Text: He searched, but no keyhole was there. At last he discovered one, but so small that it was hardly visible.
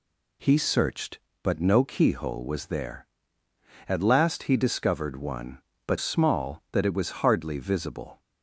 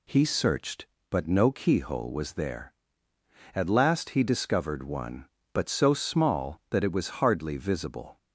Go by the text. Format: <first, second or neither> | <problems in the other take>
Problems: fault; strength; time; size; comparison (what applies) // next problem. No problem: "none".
second | skips "so"; at 5.9 s